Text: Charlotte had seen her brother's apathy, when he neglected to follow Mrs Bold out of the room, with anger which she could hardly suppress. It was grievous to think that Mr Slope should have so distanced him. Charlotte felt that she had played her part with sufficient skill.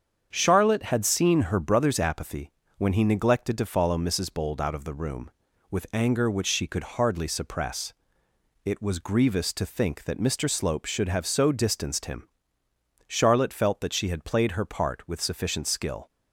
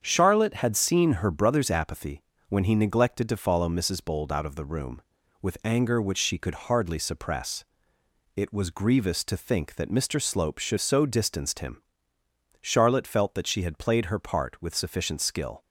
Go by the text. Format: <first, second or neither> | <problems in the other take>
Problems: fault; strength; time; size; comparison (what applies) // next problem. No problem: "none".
first | starts louder than the rest; strong; until 1.0 s; 7.5 dB; strong in the first // skips "have"; at 10.7 s